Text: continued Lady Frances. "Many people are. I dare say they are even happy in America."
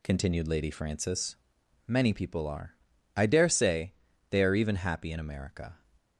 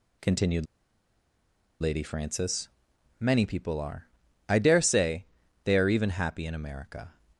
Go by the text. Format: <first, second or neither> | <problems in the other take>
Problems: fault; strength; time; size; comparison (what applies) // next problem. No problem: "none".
first | pauses between "continued" and "Lady"; at 0.6 s; 1.1 s long // pauses between "say" and "they"; at 5.2 s; 0.38 s long; also in the first